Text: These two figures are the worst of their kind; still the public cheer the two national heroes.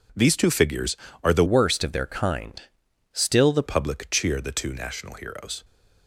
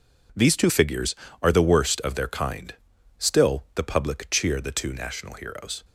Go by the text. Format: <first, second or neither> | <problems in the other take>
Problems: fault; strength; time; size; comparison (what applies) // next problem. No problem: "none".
second | changes voice from "worst" to "the"; from 1.4 to 3.6 s; 2.2 s long